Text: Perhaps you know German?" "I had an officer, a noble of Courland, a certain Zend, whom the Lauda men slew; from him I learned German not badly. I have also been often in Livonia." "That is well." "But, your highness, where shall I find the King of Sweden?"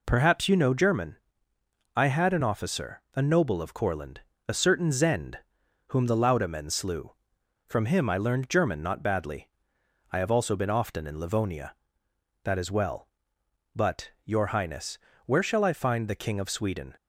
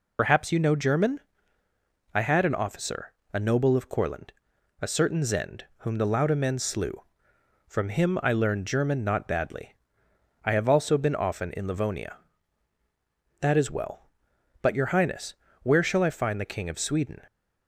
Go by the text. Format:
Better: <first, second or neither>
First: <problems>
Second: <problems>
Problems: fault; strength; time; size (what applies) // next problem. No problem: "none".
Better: first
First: none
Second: loses the start of "Perhaps"; at 0.1 s; 75 ms